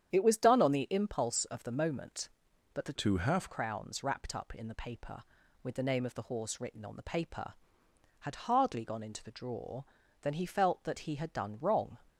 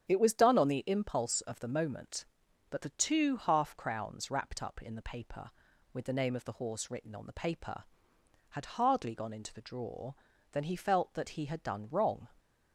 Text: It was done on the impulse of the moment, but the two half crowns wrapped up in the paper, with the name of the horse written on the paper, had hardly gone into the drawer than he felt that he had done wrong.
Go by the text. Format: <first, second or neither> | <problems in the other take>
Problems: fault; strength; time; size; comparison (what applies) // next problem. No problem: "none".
second | starts louder than the rest; strong; until 1.1 s; 9 dB; strong in the second // changes voice from "two" to "half"; from 2.9 to 3.4 s; 0.5 s long